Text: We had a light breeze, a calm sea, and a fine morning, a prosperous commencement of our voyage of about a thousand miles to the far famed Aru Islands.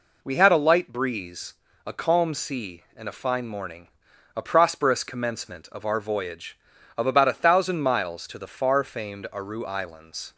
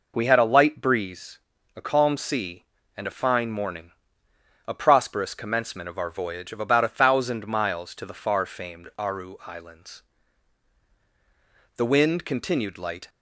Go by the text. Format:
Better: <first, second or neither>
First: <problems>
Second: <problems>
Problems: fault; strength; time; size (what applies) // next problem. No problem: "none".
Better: first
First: none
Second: goes on to say "The wind continued light"; from 11.7 s on; 1.3 s long